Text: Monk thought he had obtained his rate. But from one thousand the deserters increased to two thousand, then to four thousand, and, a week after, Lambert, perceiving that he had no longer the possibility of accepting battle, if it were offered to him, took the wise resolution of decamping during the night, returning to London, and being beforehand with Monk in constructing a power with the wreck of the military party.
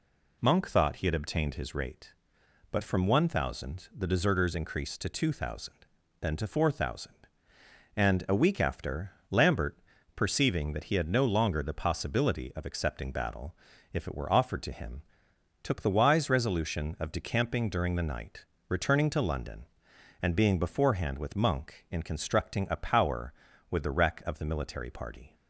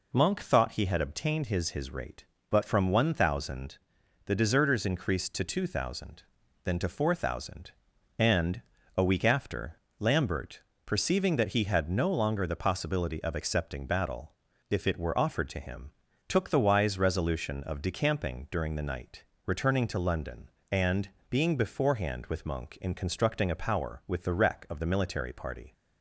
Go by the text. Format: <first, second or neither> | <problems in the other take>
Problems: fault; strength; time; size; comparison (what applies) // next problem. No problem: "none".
first | says "his" twice; at 1.7 s // pauses between "thousand" and "the"; noticeable; at 3.7 s; 0.48 s long // pauses between "and" and "being"; slight; at 21.0 s; 0.22 s long